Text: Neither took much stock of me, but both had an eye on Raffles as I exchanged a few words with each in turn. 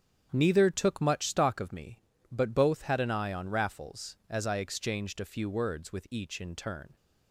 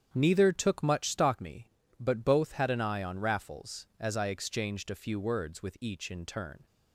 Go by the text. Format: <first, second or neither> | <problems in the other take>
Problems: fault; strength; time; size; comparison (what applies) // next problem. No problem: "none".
first | starts louder than the rest; strong; until 1.1 s; 8.5 dB; strong in the first // skips "of"; at 1.3 s